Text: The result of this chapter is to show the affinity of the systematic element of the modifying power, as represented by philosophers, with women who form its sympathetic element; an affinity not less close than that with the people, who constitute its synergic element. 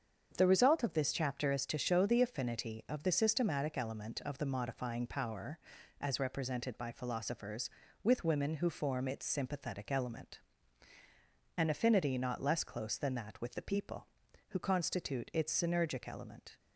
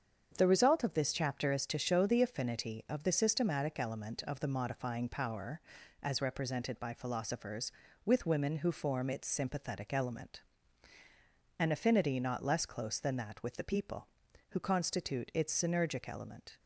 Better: neither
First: starts louder than the rest; strong; until 1.3 s; 7.5 dB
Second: starts louder than the rest; strong; until 1.3 s; 7.5 dB

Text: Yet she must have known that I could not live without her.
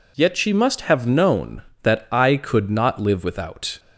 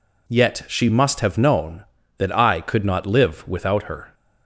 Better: second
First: stops before "her"; at 3.7 s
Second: none

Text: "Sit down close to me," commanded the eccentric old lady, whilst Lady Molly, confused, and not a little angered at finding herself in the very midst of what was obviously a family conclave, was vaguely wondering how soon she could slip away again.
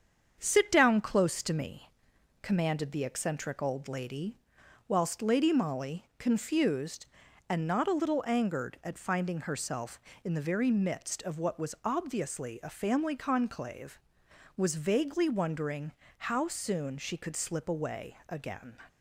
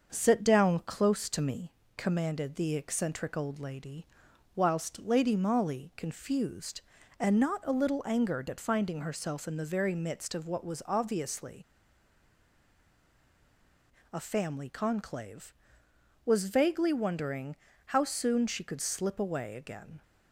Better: first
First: starts louder than the rest; strong; until 1.4 s; 7.5 dB // pauses between "wondering" and "how"; slight; at 15.9 s; 0.26 s long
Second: starts louder than the rest; until 1.1 s; 6.5 dB // pauses between "obviously" and "a"; strong; at 11.6 s; 2.4 s long // pauses between "wondering" and "how"; slight; at 17.5 s; 0.30 s long

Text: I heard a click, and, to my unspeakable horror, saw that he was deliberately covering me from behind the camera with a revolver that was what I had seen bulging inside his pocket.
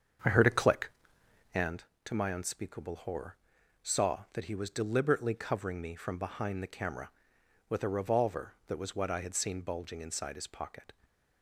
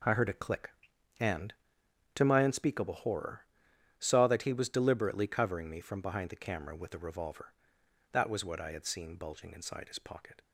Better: second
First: starts louder than the rest; strong; until 1.7 s; 7 dB // stays silent after the last word; slight; from 10.9 s on; 0.5 s long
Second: none

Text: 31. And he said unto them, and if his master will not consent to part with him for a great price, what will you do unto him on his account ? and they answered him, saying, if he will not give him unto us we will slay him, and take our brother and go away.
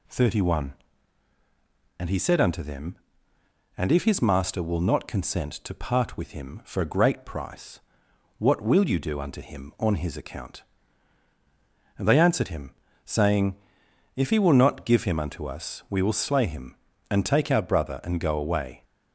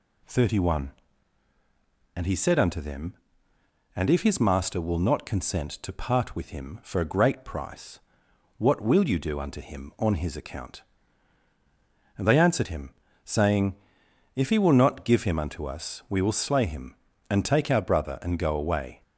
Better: neither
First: none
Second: none

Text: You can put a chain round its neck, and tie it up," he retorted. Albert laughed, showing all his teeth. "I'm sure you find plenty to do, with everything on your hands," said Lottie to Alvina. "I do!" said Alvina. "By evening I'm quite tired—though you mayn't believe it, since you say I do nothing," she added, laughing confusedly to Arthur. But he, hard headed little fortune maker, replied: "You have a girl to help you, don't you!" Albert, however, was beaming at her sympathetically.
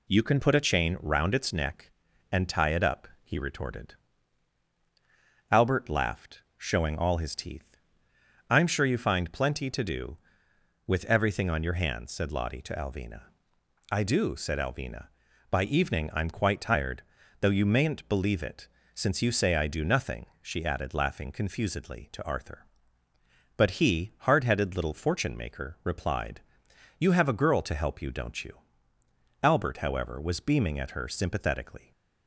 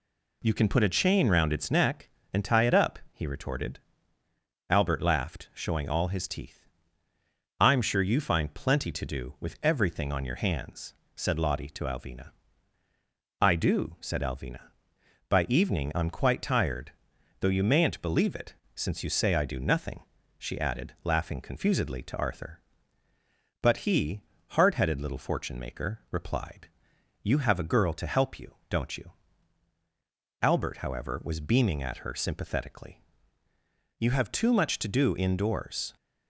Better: first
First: none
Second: goes on to say "You have too much to do indoors"; strong; from 33.9 s on; 1.9 s long

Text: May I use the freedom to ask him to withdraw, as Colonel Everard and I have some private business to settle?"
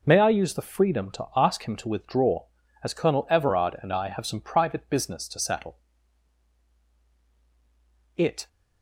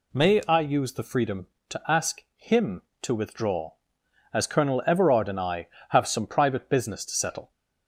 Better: second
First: goes on to say "It"; slight; from 8.1 s on; 0.32 s long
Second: none

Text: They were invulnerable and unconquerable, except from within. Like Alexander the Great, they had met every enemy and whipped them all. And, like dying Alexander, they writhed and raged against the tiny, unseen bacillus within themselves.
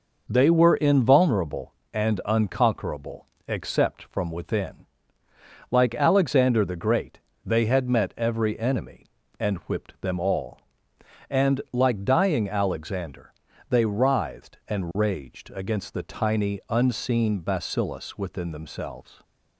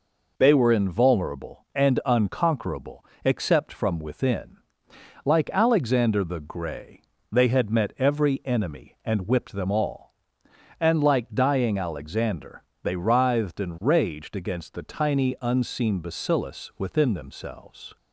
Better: first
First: none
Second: says "Grey" for "Great"; at 6.3 s

